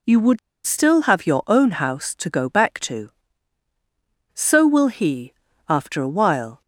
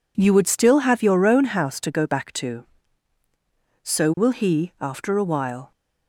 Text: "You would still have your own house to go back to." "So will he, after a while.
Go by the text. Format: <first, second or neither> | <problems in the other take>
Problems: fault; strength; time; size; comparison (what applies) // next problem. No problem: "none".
second | pauses between "would" and "still"; slight; at 0.3 s; 0.27 s long